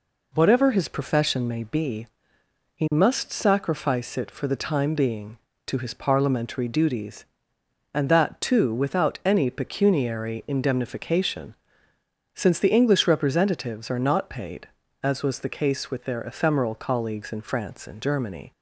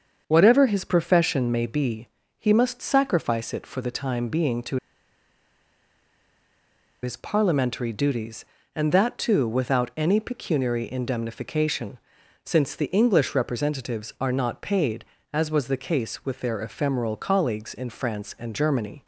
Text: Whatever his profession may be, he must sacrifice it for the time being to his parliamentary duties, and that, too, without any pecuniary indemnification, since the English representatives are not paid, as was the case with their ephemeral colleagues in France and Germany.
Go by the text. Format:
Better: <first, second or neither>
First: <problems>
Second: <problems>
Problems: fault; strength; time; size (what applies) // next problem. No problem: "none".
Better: first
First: none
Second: starts louder than the rest; until 1.2 s; 7 dB // pauses between "to" and "his"; strong; at 4.7 s; 2.2 s long